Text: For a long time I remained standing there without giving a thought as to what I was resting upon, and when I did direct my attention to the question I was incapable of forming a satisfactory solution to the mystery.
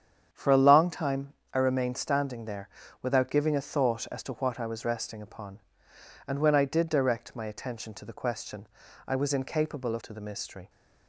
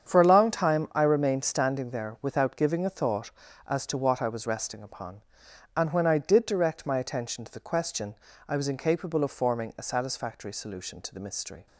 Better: second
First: starts louder than the rest; strong; until 1.3 s; 8 dB // pauses between "time" and "I"; slight; at 1.3 s; 0.20 s long // pauses between "there" and "without"; slight; at 2.6 s; 0.32 s long // pauses between "question" and "I"; at 8.6 s; 0.40 s long // skips "forming a satisfactory solution"; at 10.0 s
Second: starts louder than the rest; strong; until 1.1 s; 8 dB // pauses between "question" and "I"; slight; at 8.1 s; 0.34 s long

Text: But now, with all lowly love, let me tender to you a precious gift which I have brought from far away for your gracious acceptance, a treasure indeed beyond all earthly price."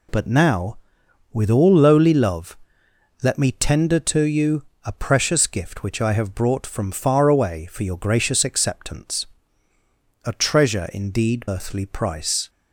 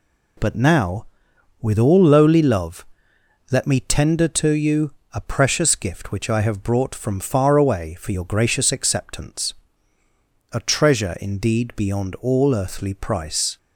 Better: second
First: pauses between "you" and "a"; slight; at 4.6 s; 0.20 s long // skips "beyond all"; at 11.4 s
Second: pauses between "you" and "a"; slight; at 4.9 s; 0.20 s long

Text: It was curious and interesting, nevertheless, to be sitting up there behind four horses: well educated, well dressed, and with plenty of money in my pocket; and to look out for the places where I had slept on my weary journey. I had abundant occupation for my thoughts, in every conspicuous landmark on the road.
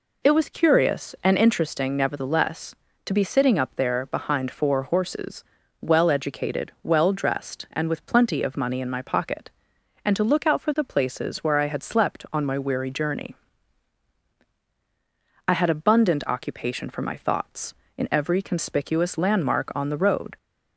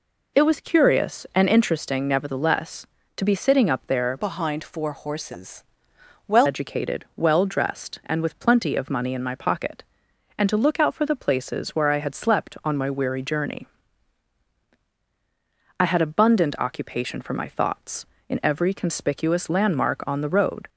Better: first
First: none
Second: changes voice from "behind" to "well"; from 4.1 to 6.4 s; 2.3 s long

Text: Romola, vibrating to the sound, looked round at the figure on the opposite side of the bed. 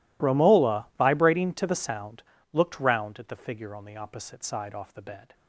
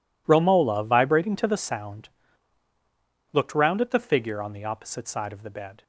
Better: second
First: says "off" for "of"; at 4.7 s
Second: none

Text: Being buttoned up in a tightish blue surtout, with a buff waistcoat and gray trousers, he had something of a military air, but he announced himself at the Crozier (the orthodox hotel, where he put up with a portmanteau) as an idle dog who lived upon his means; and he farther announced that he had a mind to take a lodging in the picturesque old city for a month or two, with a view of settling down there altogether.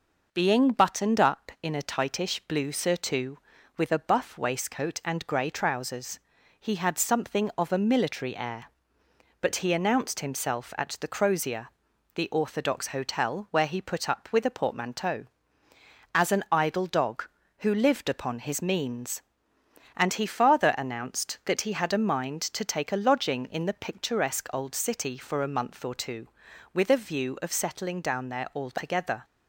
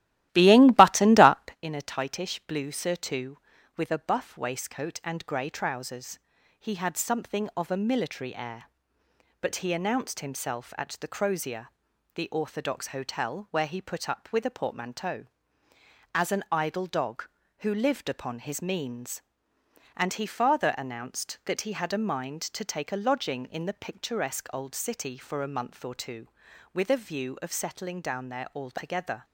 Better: first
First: none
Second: starts louder than the rest; strong; until 1.6 s; 15 dB

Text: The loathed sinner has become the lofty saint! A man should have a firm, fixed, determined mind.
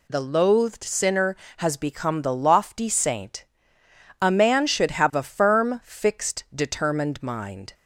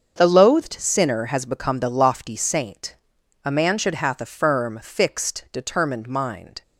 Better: first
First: none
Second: starts louder than the rest; until 1.2 s; 7 dB // says "hath" for "have"; at 3.9 s

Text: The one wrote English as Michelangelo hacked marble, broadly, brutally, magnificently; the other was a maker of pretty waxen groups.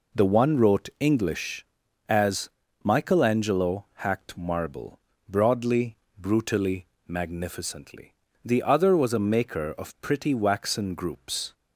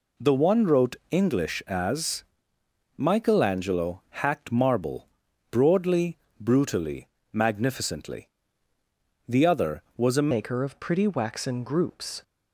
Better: first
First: pauses between "as" and "Michelangelo"; slight; at 2.5 s; 0.34 s long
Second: pauses between "wrote" and "English"; slight; at 0.9 s; 0.16 s long // pauses between "as" and "Michelangelo"; noticeable; at 2.2 s; 0.74 s long // changes voice at "maker"; from 10.3 s on; 1.9 s long

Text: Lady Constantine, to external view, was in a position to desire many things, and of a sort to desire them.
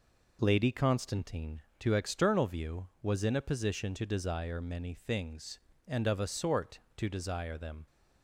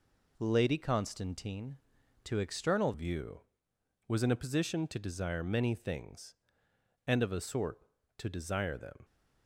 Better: first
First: none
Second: changes voice at "view"; from 2.9 s on; 6.1 s long

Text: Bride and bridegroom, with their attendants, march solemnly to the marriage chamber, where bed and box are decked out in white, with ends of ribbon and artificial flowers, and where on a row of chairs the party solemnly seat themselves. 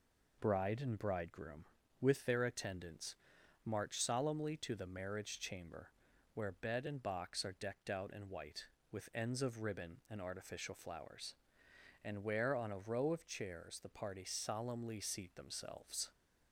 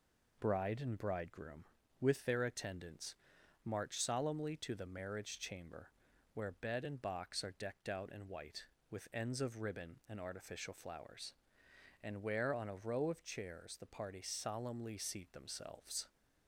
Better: neither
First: none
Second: none

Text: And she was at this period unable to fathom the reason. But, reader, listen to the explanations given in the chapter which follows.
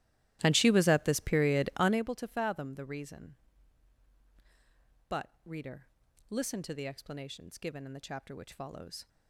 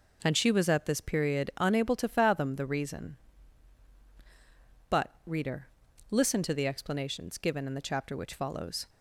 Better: second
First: starts louder than the rest; strong; until 2.1 s; 15.5 dB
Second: none

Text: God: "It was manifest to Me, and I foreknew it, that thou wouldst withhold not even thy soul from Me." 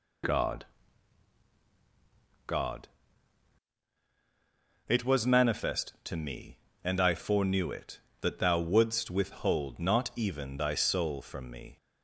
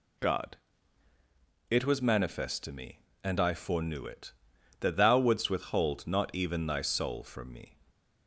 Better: second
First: says "God" twice; at 2.4 s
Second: none

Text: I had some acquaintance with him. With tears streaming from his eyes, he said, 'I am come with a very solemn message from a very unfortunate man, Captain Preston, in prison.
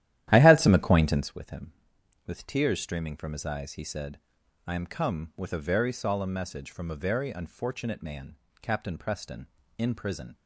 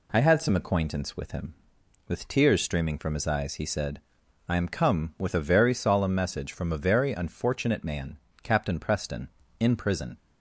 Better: second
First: starts louder than the rest; strong; until 1.3 s; 12.5 dB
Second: none

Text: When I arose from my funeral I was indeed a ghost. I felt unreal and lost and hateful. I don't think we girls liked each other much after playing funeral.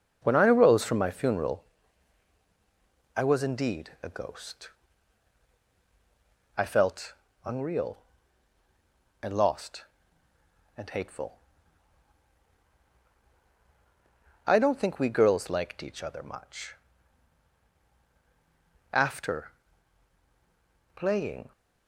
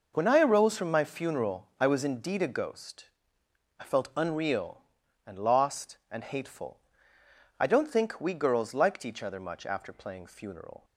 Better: second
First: pauses between "funeral" and "I"; strong; at 1.6 s; 1.5 s long // pauses between "felt" and "unreal"; slight; at 7.1 s; 0.30 s long // pauses between "much" and "after"; strong; at 16.7 s; 2.1 s long // pauses between "after" and "playing"; strong; at 19.4 s; 1.4 s long // stops before "funeral"; at 21.5 s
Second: none

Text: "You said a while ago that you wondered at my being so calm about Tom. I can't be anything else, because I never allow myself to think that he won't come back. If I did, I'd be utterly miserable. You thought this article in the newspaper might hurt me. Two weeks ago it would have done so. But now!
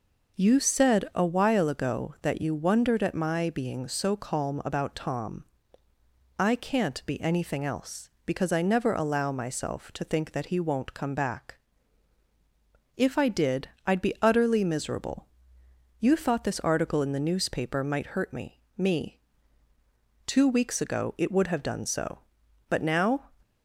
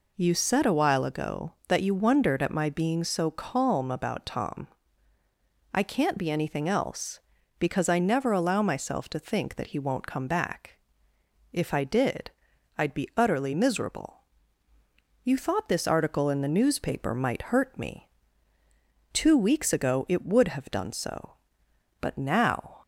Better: second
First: says "me" twice; at 18.7 s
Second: none

